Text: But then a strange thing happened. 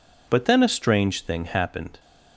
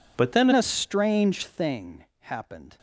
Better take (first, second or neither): first